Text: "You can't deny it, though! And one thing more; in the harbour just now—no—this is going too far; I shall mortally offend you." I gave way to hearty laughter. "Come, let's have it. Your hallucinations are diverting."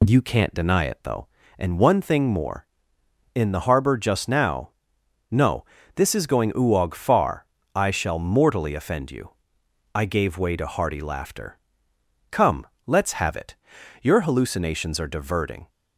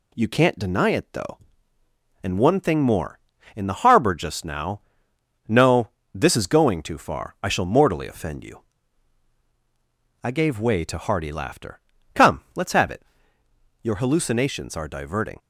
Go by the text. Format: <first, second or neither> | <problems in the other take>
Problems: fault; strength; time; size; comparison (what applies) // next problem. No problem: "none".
second | says "uog" for "too"; at 6.5 s